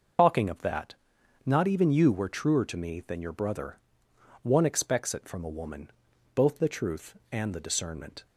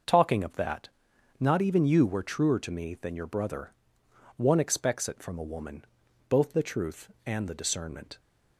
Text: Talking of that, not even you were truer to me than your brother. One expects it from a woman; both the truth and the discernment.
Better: second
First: loses the start of "Talking"; at 0.1 s; 80 ms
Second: none

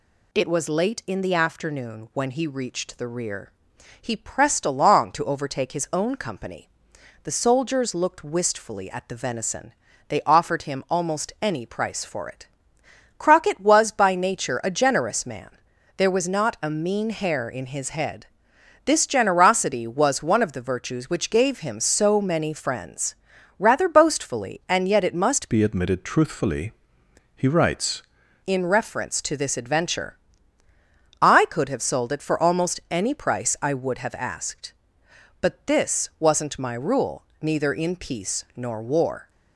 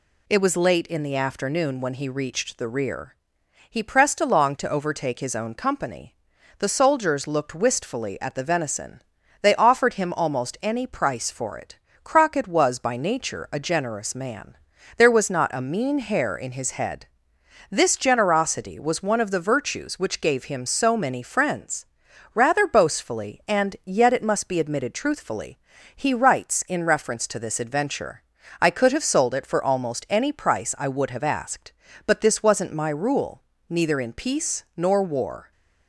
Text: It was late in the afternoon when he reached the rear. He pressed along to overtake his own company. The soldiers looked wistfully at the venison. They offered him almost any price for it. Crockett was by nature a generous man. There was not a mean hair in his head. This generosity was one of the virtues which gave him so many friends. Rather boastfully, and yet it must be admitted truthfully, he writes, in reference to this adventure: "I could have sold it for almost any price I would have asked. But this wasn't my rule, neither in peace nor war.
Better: second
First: changes voice from "be" to "writes"; from 25.4 to 28.0 s; 2.6 s long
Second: none

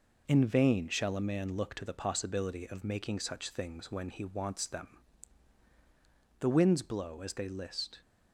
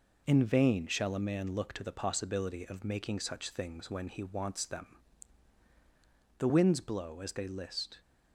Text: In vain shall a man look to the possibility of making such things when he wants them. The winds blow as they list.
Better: neither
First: none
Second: none

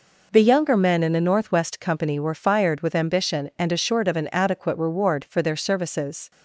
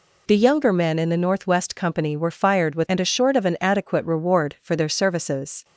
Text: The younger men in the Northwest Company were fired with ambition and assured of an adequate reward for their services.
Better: first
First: none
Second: skips "ambition"; at 2.8 s

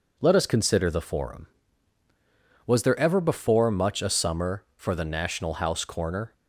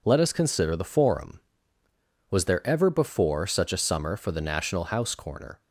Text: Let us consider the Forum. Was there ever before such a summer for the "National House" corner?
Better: second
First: says "much" for "such"; at 3.6 s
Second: none

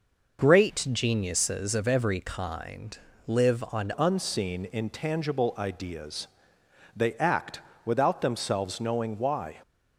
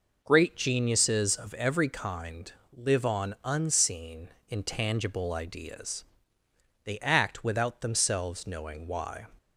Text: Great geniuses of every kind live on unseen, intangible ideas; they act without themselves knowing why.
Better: second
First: pauses between "kind" and "live"; slight; at 2.9 s; 0.30 s long // changes voice at "unseen"; from 3.9 s on; 5.6 s long // pauses between "act" and "without"; slight; at 7.5 s; 0.24 s long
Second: pauses between "kind" and "live"; slight; at 2.5 s; 0.24 s long

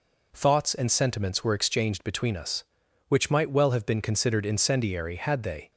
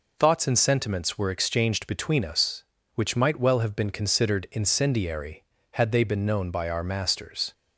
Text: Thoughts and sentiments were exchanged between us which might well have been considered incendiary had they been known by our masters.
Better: second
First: stops before "been known by our masters"; at 5.7 s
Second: none

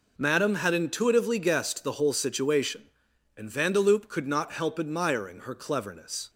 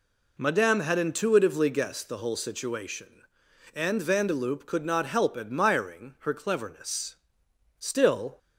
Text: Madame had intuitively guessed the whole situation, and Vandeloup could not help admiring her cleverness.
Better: first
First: none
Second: goes on to say "Still"; from 7.7 s on; 0.58 s long

